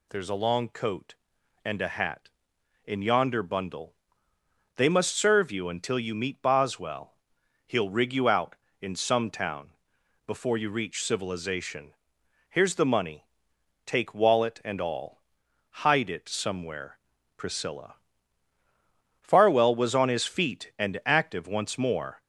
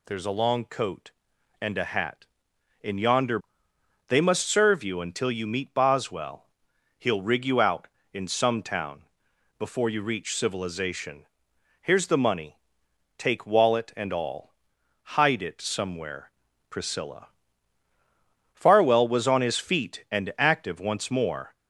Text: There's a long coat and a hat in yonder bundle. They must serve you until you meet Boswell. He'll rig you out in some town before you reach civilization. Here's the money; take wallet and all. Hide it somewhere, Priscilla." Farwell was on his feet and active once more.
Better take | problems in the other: first | skips "bundle"; at 3.7 s // pauses between "town" and "before"; noticeable; at 9.0 s; 0.56 s long; noticeable in the first

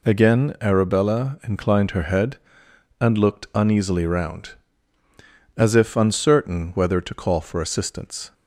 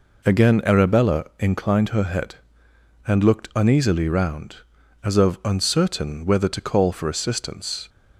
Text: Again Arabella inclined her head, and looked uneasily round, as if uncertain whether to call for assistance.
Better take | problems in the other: first | says "of" for "if"; at 5.1 s

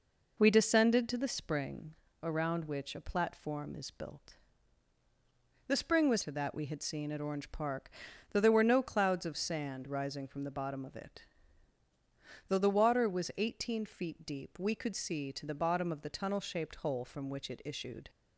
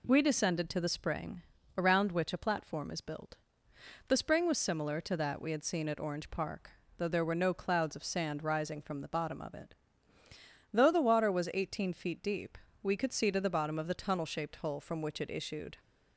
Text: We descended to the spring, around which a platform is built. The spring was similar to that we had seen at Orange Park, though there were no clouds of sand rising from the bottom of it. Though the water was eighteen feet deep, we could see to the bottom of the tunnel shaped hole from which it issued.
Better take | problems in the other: second | skips "similar"; at 6.2 s

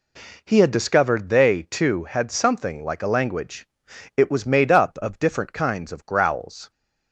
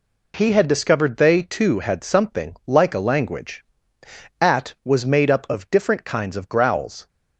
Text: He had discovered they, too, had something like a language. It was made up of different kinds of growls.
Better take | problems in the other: first | says "At" for "It"; at 4.4 s

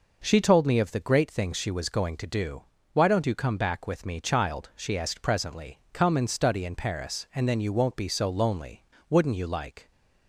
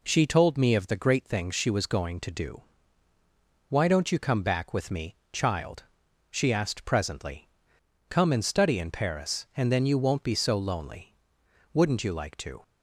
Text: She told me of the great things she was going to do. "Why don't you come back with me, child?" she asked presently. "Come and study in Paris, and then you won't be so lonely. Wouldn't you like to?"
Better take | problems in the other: second | stops before "to"; at 9.9 s

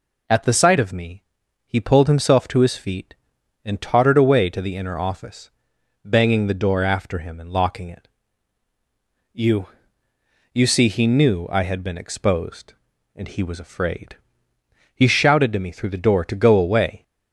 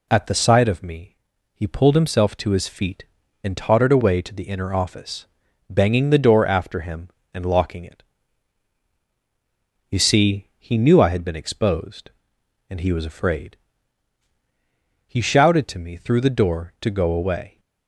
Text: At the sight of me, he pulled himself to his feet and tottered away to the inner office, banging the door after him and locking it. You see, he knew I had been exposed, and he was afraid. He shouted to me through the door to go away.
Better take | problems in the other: second | says "You" twice; at 10.5 s

